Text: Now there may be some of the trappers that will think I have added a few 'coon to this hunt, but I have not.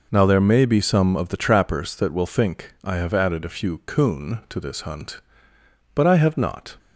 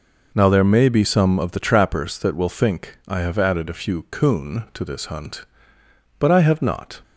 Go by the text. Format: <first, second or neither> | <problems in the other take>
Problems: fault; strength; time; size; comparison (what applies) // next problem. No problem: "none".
neither | none